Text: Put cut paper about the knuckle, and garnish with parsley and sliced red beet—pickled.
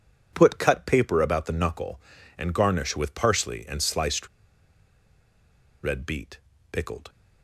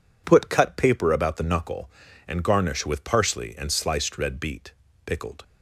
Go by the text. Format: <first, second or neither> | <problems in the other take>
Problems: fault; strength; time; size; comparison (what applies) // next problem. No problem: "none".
second | pauses between "sliced" and "red"; strong; at 4.2 s; 1.5 s long